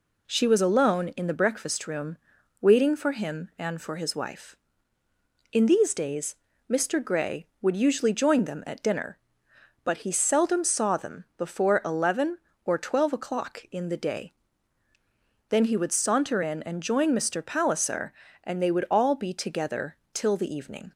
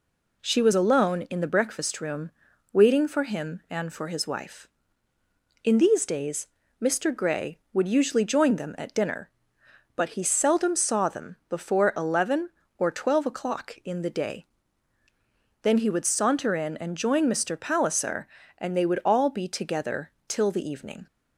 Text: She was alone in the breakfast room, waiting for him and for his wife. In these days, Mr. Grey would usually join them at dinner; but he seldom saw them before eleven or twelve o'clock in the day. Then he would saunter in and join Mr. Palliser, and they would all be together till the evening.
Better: neither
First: pauses between "together" and "till"; slight; at 19.9 s; 0.18 s long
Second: pauses between "together" and "till"; slight; at 20.1 s; 0.18 s long

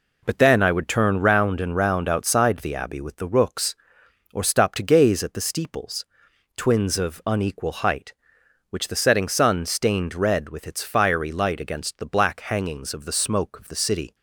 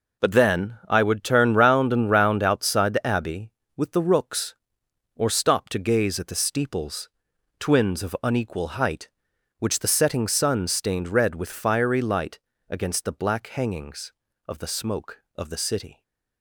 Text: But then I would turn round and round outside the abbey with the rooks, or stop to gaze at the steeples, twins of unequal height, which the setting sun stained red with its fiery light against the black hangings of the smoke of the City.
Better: first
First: none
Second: skips "its"; at 11.4 s // pauses between "light" and "against"; slight; at 12.3 s; 0.32 s long

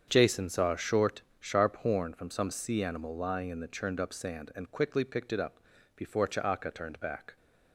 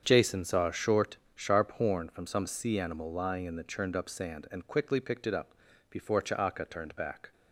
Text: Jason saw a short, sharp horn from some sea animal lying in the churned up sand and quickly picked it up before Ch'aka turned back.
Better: neither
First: starts louder than the rest; strong; until 1.0 s; 7.5 dB // pauses between "up" and "before"; at 5.5 s; 0.38 s long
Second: starts louder than the rest; strong; until 1.0 s; 7.5 dB // pauses between "up" and "before"; at 5.5 s; 0.38 s long

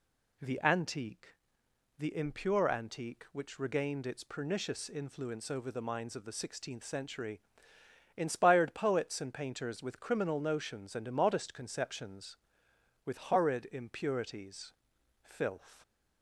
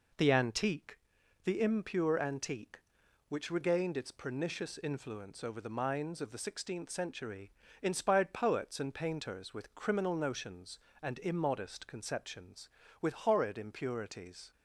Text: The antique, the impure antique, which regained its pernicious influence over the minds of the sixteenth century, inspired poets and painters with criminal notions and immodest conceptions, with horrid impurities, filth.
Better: first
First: none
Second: stops before "filth"; at 14.5 s

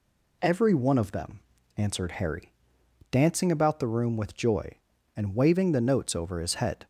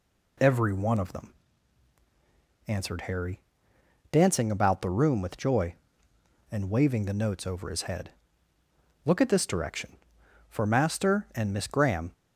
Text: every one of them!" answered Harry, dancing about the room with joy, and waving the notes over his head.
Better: first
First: none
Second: goes on to say "Look at this direction For Master and Miss Graham"; strong; from 9.0 s on; 3.0 s long

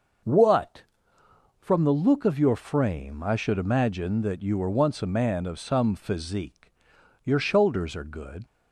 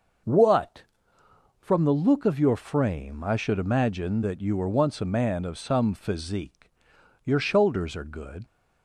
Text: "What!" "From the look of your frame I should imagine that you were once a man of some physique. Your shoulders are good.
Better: neither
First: starts louder than the rest; noticeable; until 2.0 s; 6 dB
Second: starts louder than the rest; noticeable; until 2.0 s; 6 dB

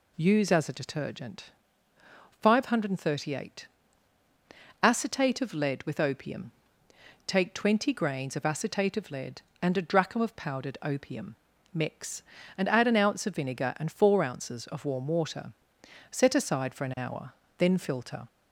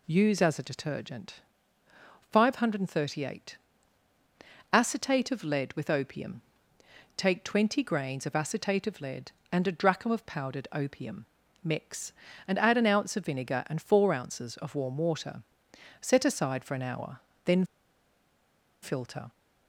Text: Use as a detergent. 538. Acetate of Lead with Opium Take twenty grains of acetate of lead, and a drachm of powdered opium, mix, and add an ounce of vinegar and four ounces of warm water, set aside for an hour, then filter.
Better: first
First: pauses between "Opium" and "Take"; noticeable; at 6.5 s; 0.74 s long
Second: pauses between "Opium" and "Take"; noticeable; at 6.4 s; 0.74 s long // pauses between "then" and "filter"; at 17.6 s; 1.1 s long

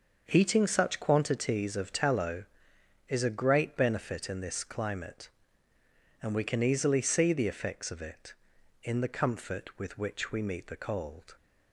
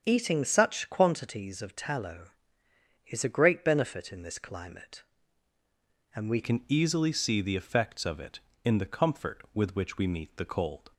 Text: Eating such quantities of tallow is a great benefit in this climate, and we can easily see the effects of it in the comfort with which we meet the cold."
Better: first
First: starts louder than the rest; until 1.2 s; 6.5 dB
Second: starts louder than the rest; strong; until 1.0 s; 7.5 dB // changes voice at "can"; from 6.4 s on; 4.5 s long

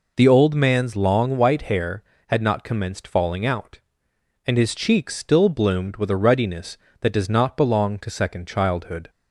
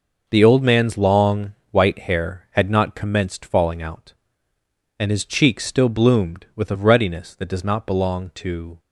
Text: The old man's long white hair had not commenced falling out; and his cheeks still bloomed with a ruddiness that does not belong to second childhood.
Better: first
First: none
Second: pauses between "long" and "white"; slight; at 1.5 s; 0.18 s long // stops before "second childhood"; at 8.7 s

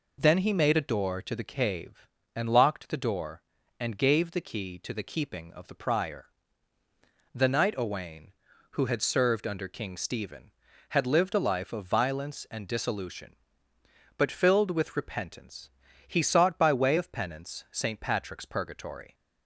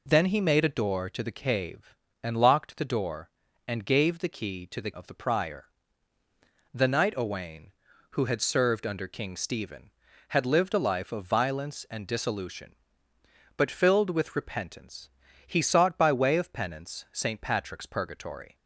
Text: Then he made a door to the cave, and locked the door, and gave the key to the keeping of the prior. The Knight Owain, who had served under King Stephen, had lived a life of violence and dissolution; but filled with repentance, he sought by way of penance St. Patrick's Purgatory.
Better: first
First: none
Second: skips "keeping"; at 4.9 s

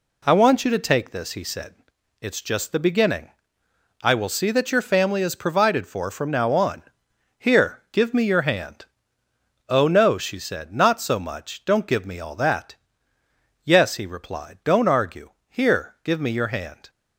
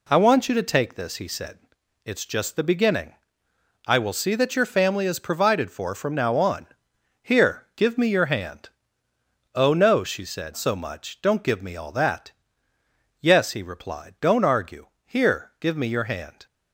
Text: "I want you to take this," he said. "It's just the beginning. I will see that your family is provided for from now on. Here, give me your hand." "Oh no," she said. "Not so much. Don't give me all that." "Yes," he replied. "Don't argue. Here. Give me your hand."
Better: first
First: none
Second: skips "Not"; at 10.5 s

